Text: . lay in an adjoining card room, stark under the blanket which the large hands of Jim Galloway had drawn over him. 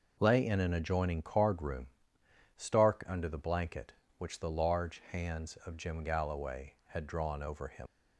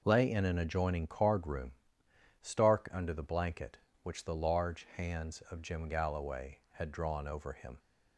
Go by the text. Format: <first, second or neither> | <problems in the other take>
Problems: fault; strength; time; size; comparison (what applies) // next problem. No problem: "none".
second | leaves "him" unfinished; at 7.8 s; 70 ms